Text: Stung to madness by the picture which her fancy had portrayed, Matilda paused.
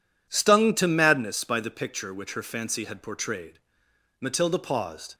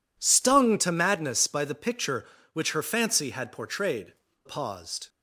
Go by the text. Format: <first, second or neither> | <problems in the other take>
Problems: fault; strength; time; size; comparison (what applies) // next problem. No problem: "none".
first | skips "Matilda"; at 4.2 s